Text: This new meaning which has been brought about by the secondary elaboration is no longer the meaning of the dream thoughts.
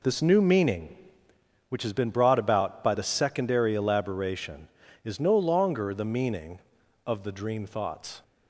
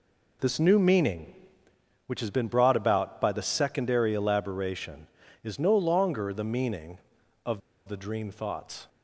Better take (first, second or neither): first